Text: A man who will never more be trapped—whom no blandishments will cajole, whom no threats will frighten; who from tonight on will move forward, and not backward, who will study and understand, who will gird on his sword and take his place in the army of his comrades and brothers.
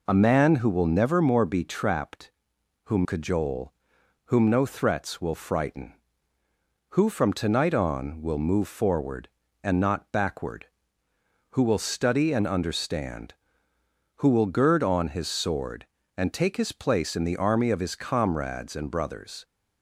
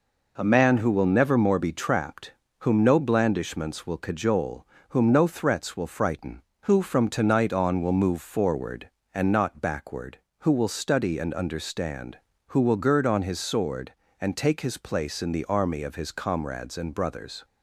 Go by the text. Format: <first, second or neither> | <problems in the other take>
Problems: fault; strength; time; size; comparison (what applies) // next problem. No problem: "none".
second | skips "no blandishments will"; at 3.0 s